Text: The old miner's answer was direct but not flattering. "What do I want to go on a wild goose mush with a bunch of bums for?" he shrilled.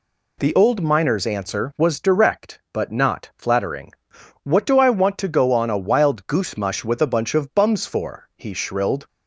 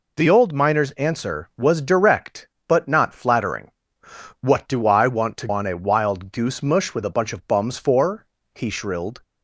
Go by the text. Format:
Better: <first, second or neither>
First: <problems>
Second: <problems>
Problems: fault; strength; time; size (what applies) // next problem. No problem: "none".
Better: first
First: none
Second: skips "go"; at 5.4 s